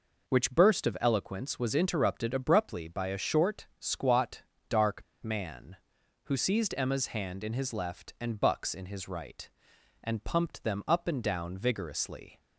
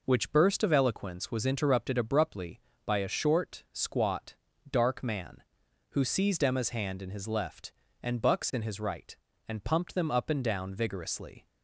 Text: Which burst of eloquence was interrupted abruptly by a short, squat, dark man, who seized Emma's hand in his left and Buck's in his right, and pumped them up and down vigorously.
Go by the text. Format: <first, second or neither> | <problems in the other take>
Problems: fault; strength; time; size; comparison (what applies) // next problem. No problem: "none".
second | pauses between "dark" and "man"; slight; at 5.0 s; 0.20 s long